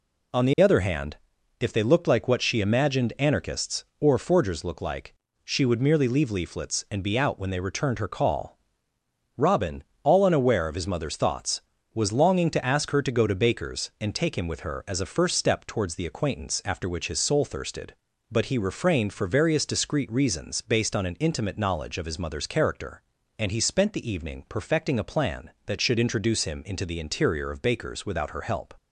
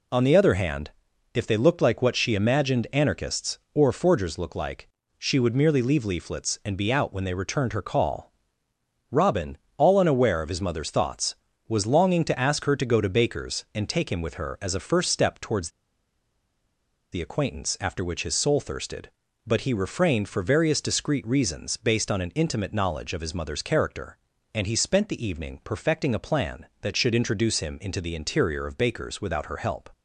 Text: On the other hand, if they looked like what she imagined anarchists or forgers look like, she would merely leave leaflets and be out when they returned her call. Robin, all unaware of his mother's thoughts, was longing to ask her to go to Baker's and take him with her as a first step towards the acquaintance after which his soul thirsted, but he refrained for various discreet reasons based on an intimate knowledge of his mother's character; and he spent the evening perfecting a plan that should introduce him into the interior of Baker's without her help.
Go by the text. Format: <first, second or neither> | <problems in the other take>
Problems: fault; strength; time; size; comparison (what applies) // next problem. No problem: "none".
first | pauses between "towards" and "the"; strong; at 15.6 s; 1.4 s long